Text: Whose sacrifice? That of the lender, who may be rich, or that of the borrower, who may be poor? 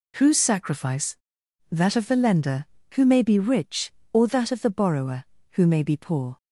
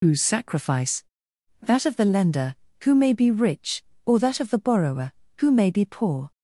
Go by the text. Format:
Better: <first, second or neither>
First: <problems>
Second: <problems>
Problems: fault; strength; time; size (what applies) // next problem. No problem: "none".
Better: first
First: none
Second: loses the start of "Whose"; at 0.0 s; 85 ms